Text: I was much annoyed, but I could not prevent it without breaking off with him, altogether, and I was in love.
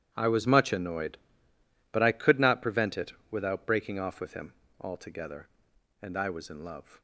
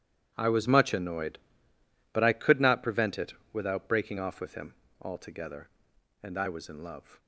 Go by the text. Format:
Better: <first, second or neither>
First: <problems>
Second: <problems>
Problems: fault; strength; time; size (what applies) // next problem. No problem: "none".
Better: neither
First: starts louder than the rest; strong; until 1.1 s; 11 dB // pauses between "it" and "without"; slight; at 3.1 s; 0.16 s long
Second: starts louder than the rest; strong; until 1.3 s; 11 dB // pauses between "it" and "without"; slight; at 3.3 s; 0.18 s long